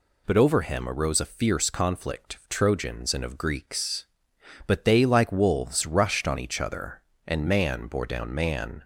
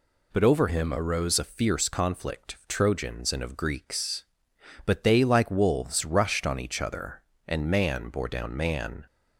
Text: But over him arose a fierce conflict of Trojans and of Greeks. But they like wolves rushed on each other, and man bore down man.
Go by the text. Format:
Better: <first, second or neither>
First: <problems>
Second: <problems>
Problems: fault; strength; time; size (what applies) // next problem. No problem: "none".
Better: first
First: none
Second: changes voice from "him" to "arose"; from 0.6 to 1.3 s; 0.7 s long